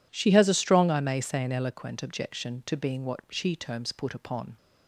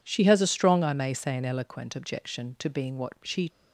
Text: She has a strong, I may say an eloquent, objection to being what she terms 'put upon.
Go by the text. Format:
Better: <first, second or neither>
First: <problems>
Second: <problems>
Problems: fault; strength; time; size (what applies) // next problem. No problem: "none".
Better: first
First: none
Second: stops before "terms put upon"; at 3.4 s